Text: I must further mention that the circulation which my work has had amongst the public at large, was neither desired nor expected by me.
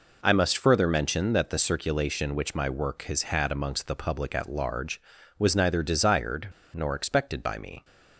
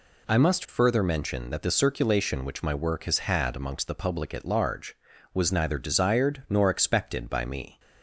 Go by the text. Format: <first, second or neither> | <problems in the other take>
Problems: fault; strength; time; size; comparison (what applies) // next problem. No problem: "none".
second | pauses between "desired" and "nor"; slight; at 6.4 s; 0.25 s long